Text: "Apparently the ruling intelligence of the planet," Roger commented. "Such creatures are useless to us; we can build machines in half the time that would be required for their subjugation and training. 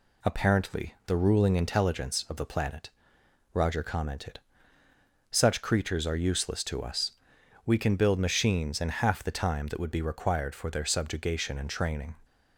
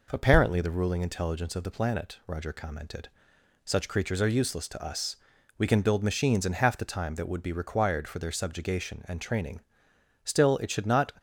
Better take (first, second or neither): first